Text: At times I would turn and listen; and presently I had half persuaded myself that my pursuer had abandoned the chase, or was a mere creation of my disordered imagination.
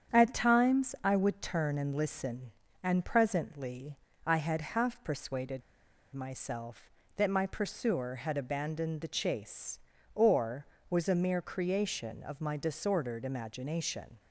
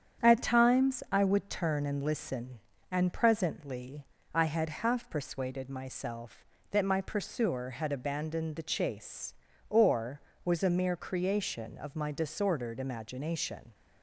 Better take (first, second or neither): second